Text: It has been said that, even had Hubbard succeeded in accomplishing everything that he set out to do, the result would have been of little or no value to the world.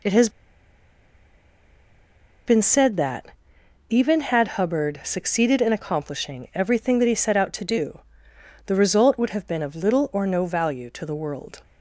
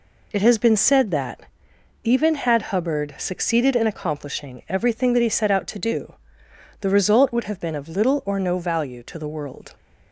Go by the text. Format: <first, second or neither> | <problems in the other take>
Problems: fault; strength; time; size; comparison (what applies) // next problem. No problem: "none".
second | pauses between "has" and "been"; strong; at 0.2 s; 2.1 s long